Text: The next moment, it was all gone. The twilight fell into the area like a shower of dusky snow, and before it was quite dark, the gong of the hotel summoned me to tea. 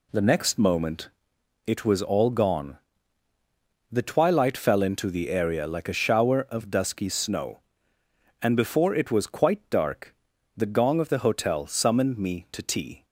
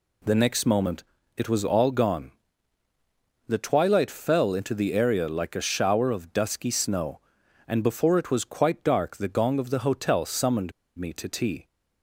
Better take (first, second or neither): first